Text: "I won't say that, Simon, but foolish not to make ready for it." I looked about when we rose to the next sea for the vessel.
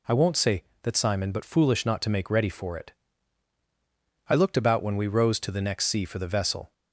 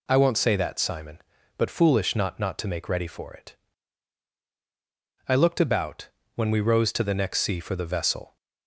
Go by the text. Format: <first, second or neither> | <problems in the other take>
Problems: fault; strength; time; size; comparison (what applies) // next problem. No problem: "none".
first | says "not" twice; at 2.3 s // pauses between "about" and "when"; slight; at 6.1 s; 0.26 s long